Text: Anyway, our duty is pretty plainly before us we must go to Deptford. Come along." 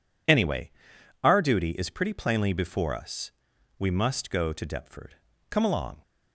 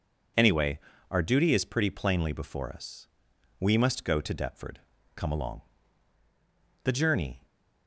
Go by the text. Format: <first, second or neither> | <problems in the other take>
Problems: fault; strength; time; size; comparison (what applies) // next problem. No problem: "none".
first | pauses between "us" and "we"; noticeable; at 3.0 s; 0.50 s long; noticeable in the first // goes on to say "The journey"; noticeable; from 6.8 s on; 0.62 s long